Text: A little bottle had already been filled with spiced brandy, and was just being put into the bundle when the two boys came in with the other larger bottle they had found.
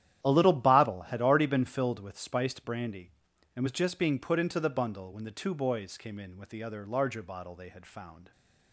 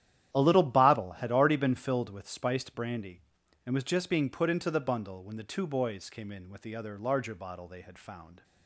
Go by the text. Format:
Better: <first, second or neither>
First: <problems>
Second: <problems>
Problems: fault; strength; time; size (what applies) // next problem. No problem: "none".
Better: neither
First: starts louder than the rest; strong; until 1.2 s; 11 dB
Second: starts louder than the rest; strong; until 1.3 s; 11 dB